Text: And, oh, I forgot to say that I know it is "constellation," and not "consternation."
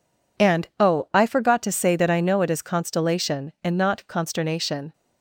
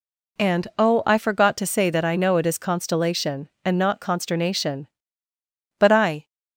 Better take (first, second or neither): first